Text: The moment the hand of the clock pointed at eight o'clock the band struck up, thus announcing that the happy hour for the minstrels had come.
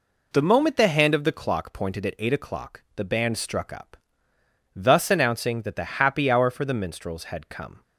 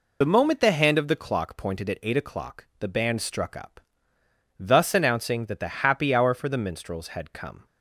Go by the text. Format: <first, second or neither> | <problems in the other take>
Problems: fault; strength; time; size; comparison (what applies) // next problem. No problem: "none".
first | loses the start of "The"; at 0.2 s; 45 ms